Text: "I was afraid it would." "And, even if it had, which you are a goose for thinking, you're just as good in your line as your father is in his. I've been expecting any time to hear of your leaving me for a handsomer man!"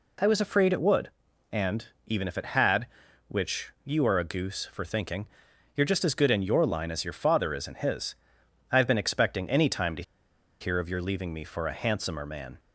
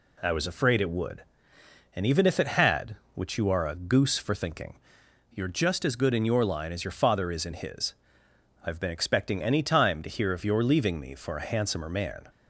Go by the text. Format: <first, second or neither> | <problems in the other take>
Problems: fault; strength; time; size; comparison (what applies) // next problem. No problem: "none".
second | pauses between "to" and "hear"; noticeable; at 10.0 s; 0.57 s long